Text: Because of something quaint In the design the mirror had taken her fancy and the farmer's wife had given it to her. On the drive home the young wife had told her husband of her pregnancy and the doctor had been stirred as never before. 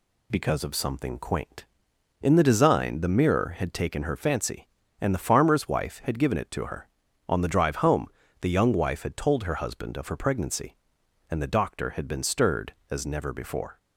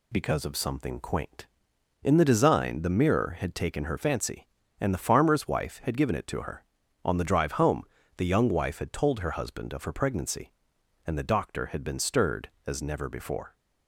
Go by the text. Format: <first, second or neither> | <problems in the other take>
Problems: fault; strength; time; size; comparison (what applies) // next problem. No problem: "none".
neither | pauses between "home" and "the"; slight; the same in both